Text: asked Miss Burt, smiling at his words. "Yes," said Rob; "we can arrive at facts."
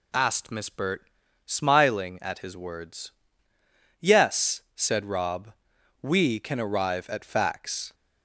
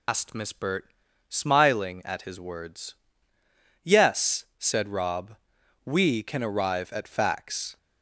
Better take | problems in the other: first | loses the start of "asked"; at 0.0 s; 110 ms

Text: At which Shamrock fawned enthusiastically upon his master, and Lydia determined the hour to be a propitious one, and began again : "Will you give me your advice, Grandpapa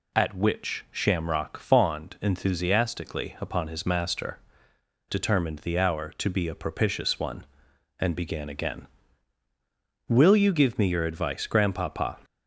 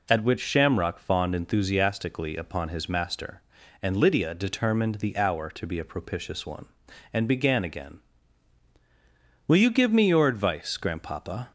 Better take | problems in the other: second | skips "and Lydia"; at 4.7 s

